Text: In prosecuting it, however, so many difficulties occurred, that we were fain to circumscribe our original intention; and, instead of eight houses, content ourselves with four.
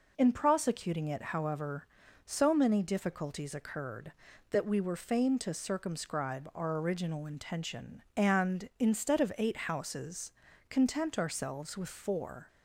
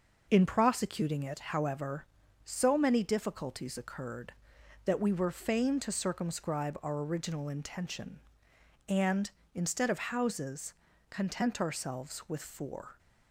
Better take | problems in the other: first | skips "eight"; at 10.0 s

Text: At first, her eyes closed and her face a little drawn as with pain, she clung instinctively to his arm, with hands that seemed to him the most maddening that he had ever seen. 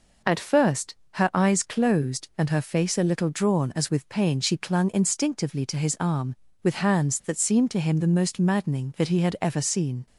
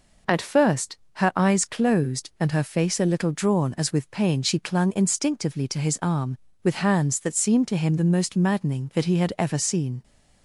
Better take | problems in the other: neither | none

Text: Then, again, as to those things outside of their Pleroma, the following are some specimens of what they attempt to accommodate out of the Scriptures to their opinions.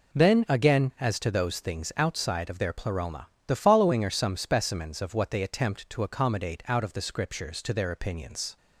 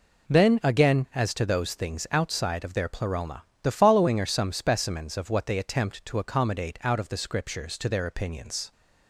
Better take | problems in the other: neither | none

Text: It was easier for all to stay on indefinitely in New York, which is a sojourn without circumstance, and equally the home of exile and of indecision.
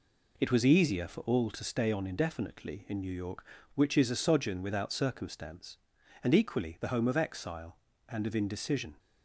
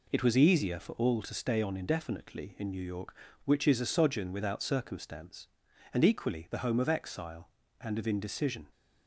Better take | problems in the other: neither | none

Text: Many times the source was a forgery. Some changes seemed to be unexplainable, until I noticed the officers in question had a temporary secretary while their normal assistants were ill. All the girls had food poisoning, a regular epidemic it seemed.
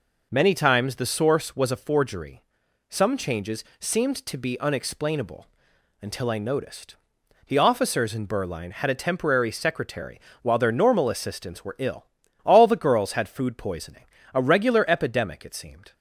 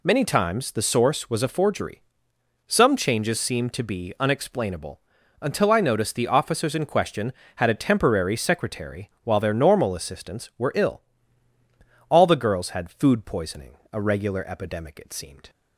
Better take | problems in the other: second | pauses between "noticed" and "the"; noticeable; at 6.9 s; 0.52 s long // says "berline" for "question"; at 8.2 s // pauses between "secretary" and "while"; slight; at 10.1 s; 0.24 s long

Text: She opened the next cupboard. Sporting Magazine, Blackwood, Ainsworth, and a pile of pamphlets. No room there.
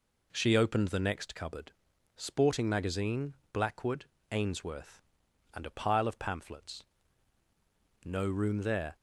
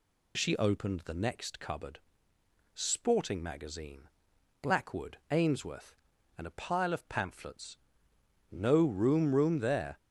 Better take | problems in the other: first | says "room" twice; at 9.3 s

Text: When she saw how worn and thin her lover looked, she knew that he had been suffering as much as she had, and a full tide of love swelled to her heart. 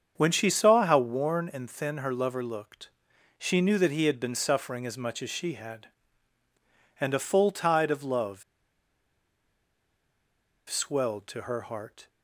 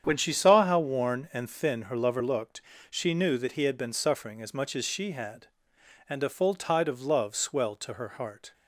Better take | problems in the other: second | starts louder than the rest; strong; until 1.1 s; 7.5 dB; strong in the second // pauses between "love" and "swelled"; strong; at 8.4 s; 2.2 s long

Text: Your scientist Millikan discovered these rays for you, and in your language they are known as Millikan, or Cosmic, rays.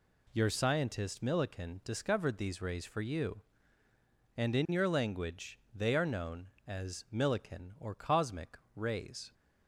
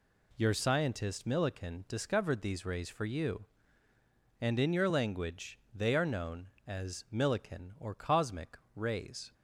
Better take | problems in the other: neither | pauses between "language" and "they"; slight; the same in both

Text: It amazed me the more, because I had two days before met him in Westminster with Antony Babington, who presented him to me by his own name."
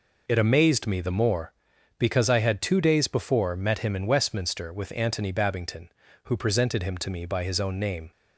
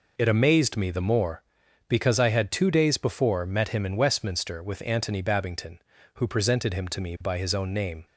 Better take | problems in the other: neither | none

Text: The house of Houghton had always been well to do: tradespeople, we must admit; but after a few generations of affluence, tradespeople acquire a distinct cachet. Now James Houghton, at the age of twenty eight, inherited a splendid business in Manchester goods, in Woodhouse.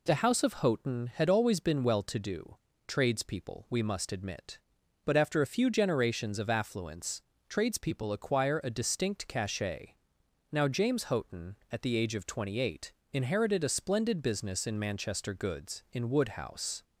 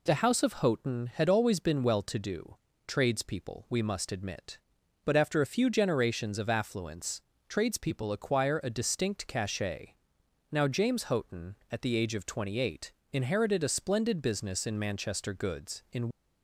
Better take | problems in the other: first | stops before "Woodhouse"; at 16.1 s

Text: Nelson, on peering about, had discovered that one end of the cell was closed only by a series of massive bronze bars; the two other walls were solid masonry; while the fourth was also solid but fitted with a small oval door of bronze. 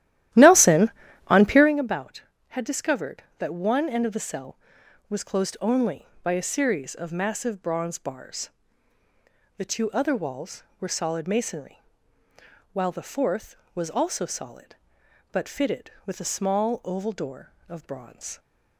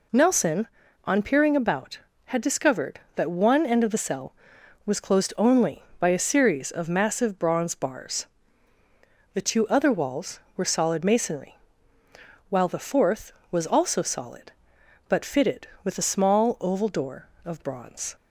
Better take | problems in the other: second | starts louder than the rest; strong; until 1.7 s; 13.5 dB

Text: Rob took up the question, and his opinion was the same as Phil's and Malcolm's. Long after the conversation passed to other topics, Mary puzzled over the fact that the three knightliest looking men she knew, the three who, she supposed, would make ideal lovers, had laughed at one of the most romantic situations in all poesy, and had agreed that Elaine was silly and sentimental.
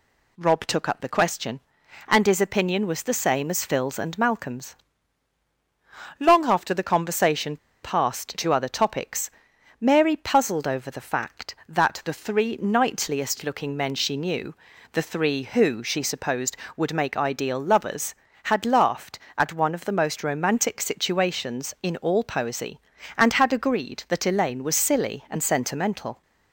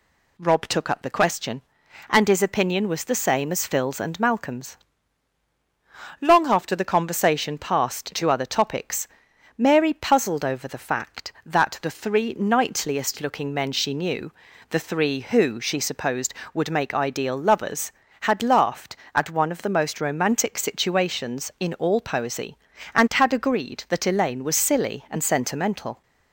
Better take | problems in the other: second | pauses between "conversation" and "passed"; slight; at 7.5 s; 0.27 s long

